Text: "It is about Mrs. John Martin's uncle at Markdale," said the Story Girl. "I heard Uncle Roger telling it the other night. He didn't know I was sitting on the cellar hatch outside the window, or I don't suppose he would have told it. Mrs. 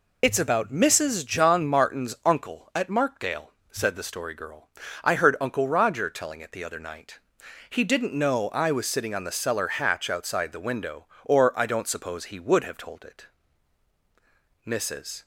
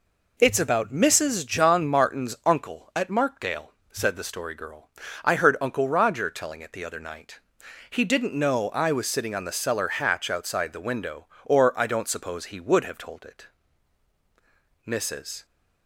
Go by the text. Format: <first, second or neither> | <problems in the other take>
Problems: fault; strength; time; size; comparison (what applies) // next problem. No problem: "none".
second | loses the start of "It"; at 0.2 s; 50 ms